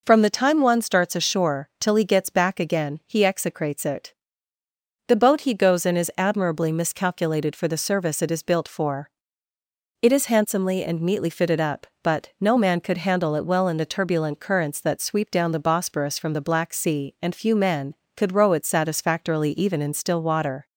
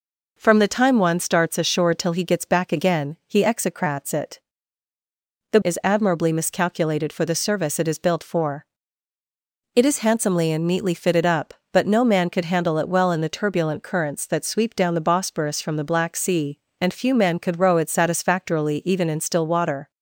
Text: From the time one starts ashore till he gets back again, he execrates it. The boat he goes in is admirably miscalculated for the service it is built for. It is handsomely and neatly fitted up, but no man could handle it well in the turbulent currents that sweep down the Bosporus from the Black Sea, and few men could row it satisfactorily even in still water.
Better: first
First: none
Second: skips "boat he goes in"; at 5.6 s

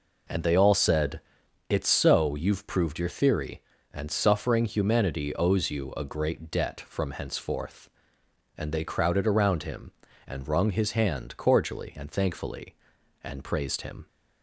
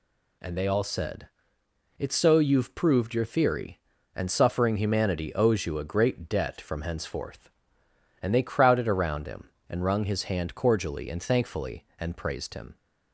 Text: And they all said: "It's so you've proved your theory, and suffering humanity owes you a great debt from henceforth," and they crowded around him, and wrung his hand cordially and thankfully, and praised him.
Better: second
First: starts louder than the rest; noticeable; until 1.6 s; 4.5 dB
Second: none

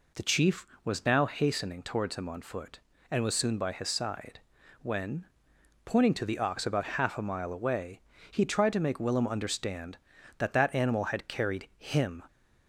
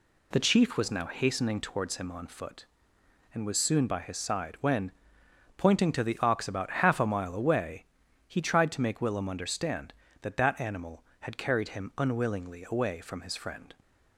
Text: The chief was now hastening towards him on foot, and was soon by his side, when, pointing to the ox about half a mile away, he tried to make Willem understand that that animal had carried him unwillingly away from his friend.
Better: second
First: stops before "unwillingly away from his friend"; at 12.2 s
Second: none

